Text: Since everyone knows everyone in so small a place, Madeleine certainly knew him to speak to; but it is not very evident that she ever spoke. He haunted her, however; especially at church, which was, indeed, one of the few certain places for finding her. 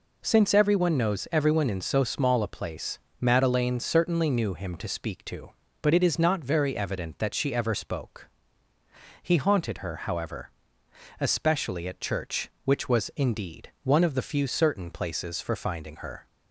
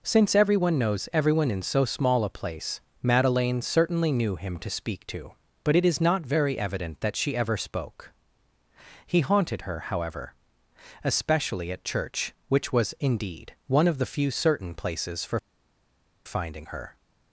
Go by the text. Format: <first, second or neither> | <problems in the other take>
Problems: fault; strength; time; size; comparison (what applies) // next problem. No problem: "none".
first | pauses between "for" and "finding"; noticeable; at 15.3 s; 0.87 s long